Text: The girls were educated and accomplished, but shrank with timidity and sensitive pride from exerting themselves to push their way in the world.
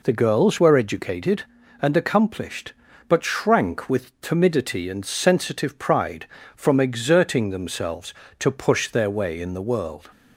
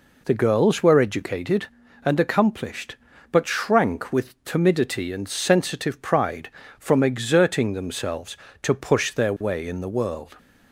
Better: neither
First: none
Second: none

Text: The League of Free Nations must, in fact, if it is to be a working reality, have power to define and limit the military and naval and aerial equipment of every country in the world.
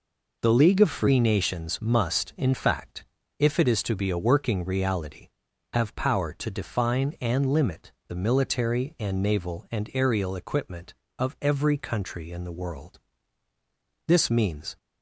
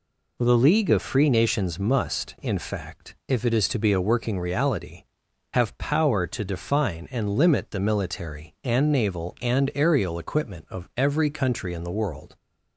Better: second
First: pauses between "limit" and "the"; slight; at 7.9 s; 0.16 s long // goes on to say "This means"; noticeable; from 14.0 s on; 0.70 s long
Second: none

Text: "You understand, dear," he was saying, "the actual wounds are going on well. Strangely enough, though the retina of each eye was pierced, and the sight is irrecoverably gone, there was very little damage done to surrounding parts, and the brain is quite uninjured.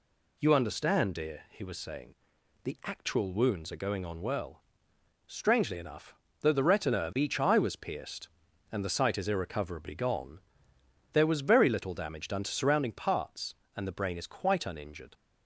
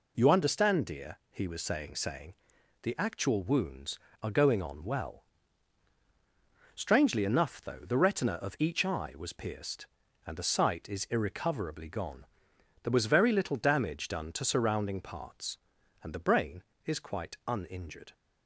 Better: first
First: none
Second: says "saying" twice; at 1.9 s

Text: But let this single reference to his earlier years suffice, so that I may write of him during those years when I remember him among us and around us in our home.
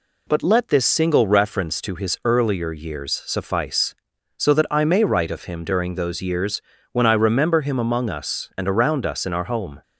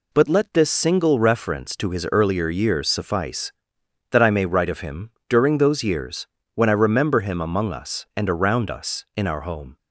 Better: first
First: pauses between "years" and "when"; slight; at 6.5 s; 0.32 s long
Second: skips "so"; at 3.7 s // pauses between "him" and "during"; slight; at 5.0 s; 0.20 s long // pauses between "years" and "when"; slight; at 6.2 s; 0.28 s long

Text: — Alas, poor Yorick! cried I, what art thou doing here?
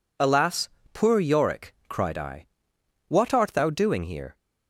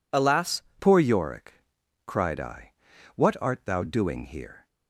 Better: first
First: none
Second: changes voice at "poor"; from 0.7 s on; 3.9 s long

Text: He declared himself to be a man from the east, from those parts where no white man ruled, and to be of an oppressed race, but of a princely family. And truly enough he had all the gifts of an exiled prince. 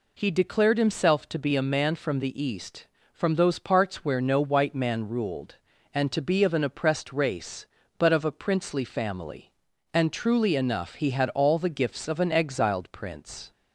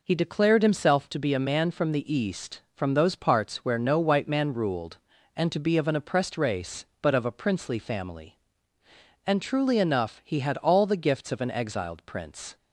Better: neither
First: none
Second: none

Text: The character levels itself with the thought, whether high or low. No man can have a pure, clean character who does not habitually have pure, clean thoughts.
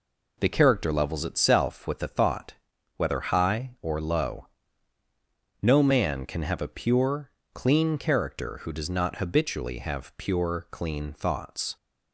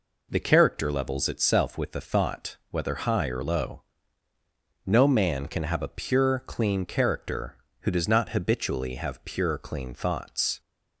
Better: neither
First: none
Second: none

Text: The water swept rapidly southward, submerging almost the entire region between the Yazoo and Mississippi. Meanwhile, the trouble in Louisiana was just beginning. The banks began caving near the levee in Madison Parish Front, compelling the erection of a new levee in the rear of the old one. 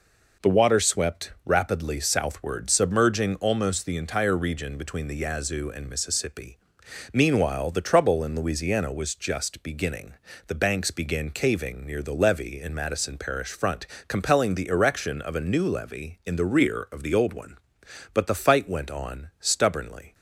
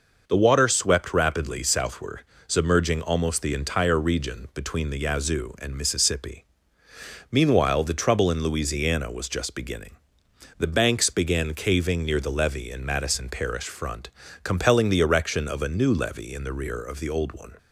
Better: second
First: goes on to say "But the fight went on stubbornly"; strong; from 18.1 s on; 2.0 s long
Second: none

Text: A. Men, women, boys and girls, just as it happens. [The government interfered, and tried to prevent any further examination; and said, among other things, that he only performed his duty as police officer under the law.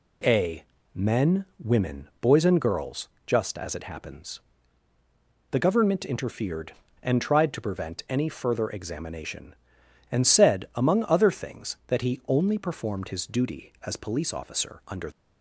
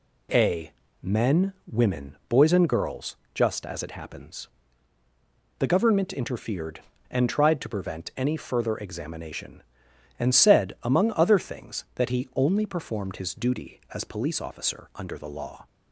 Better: second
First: stops before "the law"; at 15.1 s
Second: none

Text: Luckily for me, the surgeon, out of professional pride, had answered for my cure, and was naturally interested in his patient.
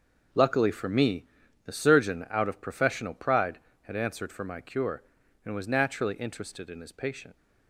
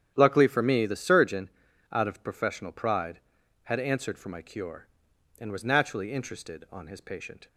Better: first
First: starts louder than the rest; until 1.7 s; 6 dB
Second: starts louder than the rest; strong; until 1.1 s; 9.5 dB // says "on" for "in"; at 6.6 s

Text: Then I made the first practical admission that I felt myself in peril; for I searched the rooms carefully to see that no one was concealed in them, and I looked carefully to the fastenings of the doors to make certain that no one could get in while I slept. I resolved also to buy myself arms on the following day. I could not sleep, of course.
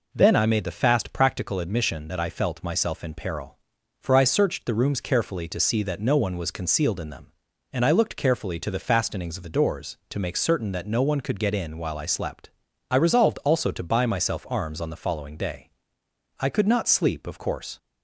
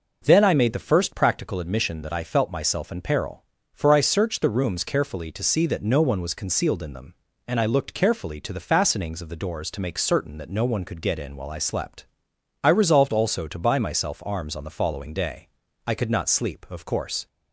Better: second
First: says "fast" for "first"; at 0.7 s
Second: none

